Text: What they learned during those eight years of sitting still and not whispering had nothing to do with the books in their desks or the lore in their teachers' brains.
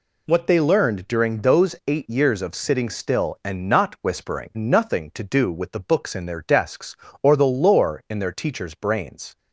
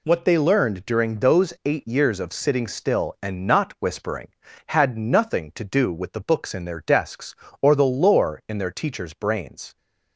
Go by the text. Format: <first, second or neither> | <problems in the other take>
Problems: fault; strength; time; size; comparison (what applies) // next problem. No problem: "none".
second | skips "had"; at 4.5 s